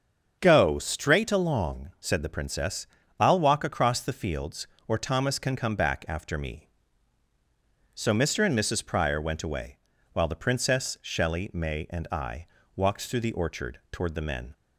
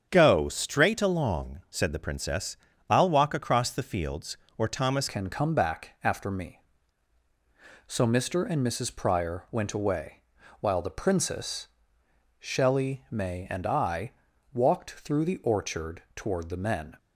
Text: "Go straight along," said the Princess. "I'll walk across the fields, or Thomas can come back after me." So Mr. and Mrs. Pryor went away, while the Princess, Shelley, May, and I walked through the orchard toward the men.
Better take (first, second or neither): first